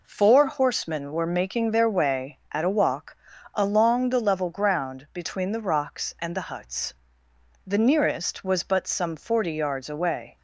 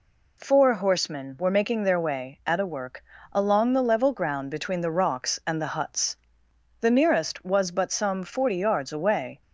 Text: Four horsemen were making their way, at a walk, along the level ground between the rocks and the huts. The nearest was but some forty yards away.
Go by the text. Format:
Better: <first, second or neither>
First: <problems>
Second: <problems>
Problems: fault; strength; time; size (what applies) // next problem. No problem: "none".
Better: first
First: none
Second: says "work" for "walk"; at 2.6 s